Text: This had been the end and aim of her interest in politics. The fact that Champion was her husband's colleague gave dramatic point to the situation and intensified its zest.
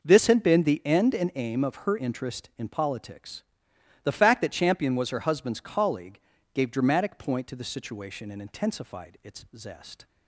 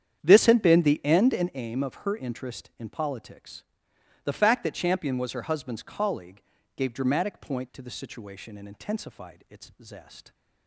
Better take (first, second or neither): first